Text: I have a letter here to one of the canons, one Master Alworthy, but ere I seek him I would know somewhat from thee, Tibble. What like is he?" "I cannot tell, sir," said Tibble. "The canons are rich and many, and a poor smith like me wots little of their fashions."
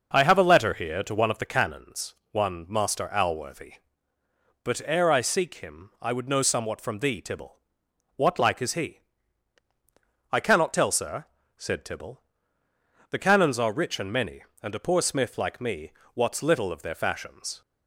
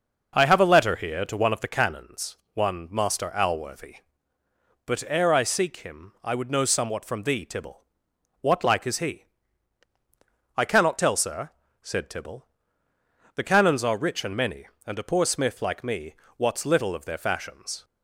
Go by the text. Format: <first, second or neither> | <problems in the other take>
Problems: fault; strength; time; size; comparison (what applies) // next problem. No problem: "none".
neither | pauses between "me" and "wots"; slight; the same in both